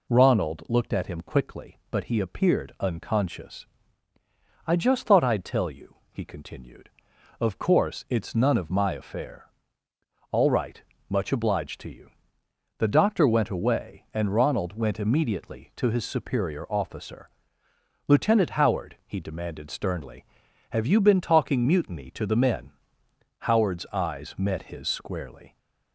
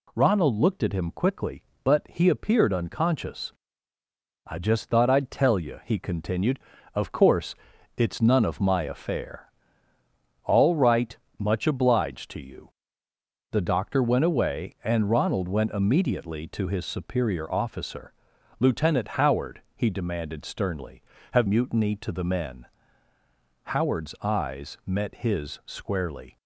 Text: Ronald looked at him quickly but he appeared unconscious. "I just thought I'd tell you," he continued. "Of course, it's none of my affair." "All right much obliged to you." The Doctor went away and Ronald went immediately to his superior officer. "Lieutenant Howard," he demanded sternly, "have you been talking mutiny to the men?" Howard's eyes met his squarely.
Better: first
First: pauses between "right" and "much"; slight; at 10.8 s; 0.30 s long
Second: pauses between "right" and "much"; slight; at 11.1 s; 0.22 s long // skips "you been talking"; at 21.4 s

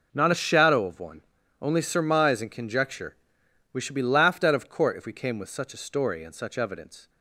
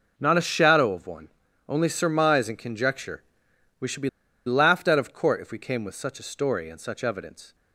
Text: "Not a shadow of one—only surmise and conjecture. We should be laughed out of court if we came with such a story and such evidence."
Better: first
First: none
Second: pauses between "be" and "laughed"; at 4.0 s; 0.37 s long

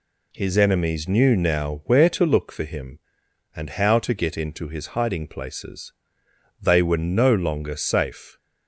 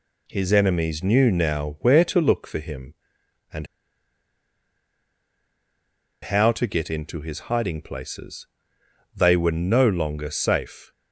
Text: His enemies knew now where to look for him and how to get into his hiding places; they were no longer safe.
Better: first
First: none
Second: pauses between "and" and "how"; strong; at 3.6 s; 2.5 s long

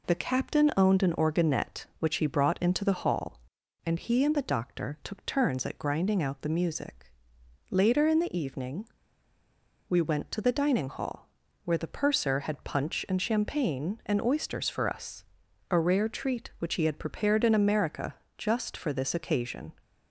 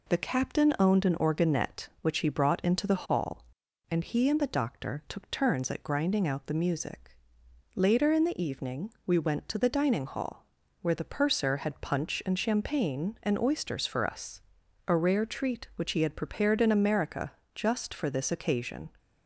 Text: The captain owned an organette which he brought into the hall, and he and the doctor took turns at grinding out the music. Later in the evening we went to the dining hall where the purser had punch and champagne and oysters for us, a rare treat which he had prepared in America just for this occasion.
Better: second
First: pauses between "evening" and "we"; at 8.8 s; 1.0 s long // pauses between "hall" and "where"; slight; at 11.2 s; 0.36 s long // pauses between "America" and "just"; slight; at 18.1 s; 0.22 s long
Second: pauses between "hall" and "where"; slight; at 10.4 s; 0.36 s long // pauses between "America" and "just"; slight; at 17.3 s; 0.22 s long

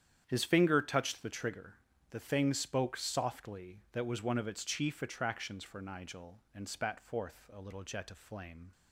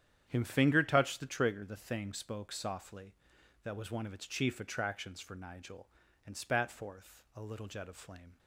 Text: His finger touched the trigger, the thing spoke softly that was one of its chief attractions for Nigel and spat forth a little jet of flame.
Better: first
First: starts louder than the rest; strong; until 1.2 s; 9.5 dB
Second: starts louder than the rest; strong; until 1.2 s; 9.5 dB // says "Him" for "His"; at 0.2 s

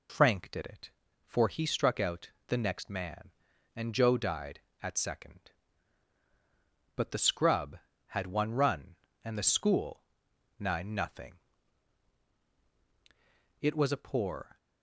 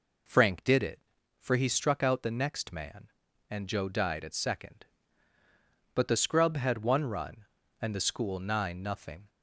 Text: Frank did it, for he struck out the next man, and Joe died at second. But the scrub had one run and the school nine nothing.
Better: second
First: pauses between "out" and "the"; slight; at 2.3 s; 0.18 s long // pauses between "school" and "nine"; noticeable; at 10.0 s; 0.56 s long // goes on to say "It was a poor"; noticeable; from 13.6 s on; 0.96 s long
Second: none

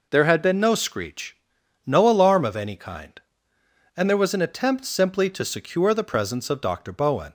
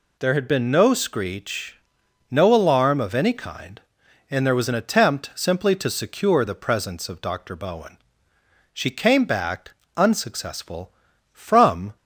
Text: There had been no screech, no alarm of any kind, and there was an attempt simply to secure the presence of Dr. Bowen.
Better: first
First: none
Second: goes on to say "She came back unsuccessful from"; strong; from 8.7 s on; 3.2 s long

